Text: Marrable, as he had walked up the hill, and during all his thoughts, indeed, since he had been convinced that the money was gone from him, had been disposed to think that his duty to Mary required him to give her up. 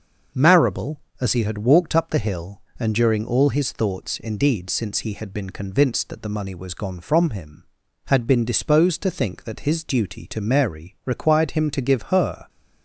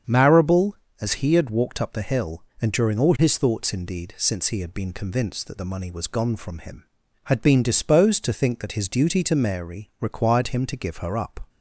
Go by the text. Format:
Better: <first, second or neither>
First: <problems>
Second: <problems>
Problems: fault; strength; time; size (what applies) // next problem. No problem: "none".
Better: second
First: starts louder than the rest; until 1.5 s; 6 dB // stops before "up"; at 12.4 s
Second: starts louder than the rest; strong; until 1.3 s; 7.5 dB